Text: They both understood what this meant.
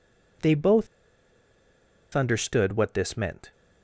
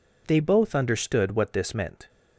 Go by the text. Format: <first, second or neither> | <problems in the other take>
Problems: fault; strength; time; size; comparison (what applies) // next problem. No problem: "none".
second | pauses between "both" and "understood"; strong; at 0.8 s; 1.2 s long